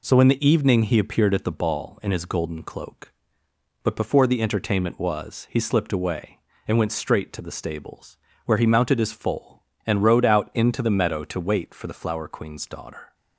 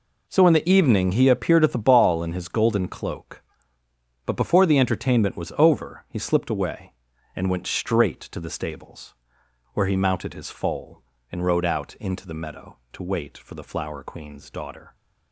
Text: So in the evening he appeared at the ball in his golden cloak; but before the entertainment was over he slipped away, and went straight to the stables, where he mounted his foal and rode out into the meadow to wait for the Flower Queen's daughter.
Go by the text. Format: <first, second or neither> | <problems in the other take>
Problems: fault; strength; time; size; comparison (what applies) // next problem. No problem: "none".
second | skips "over"; at 5.4 s